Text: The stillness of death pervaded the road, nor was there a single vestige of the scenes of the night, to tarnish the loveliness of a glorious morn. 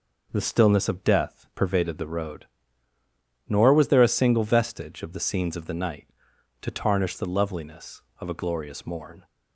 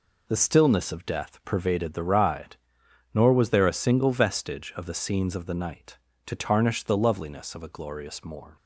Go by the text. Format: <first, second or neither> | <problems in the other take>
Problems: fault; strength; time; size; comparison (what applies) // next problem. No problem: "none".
first | says "ride" for "road"; at 2.0 s